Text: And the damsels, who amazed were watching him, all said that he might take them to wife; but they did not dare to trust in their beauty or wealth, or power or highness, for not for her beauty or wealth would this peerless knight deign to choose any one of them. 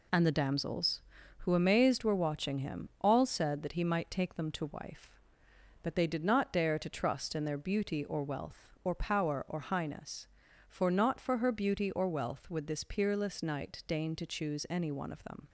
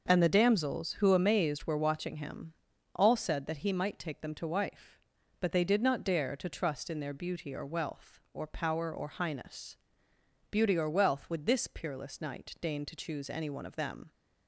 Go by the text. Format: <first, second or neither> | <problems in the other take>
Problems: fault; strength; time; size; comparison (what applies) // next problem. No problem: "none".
first | starts louder than the rest; noticeable; until 1.0 s; 6 dB // skips "for not for her"; at 10.1 s